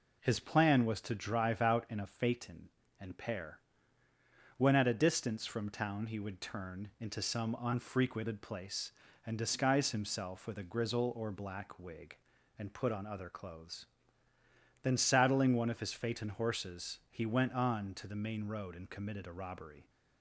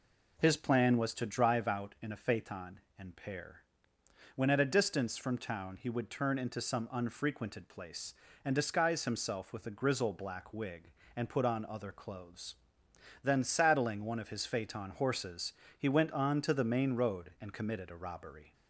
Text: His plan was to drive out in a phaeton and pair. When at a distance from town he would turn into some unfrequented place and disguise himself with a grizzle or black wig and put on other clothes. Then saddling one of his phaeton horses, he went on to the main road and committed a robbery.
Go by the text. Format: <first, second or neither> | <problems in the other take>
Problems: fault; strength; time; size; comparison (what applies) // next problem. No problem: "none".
first | skips "or"; at 10.1 s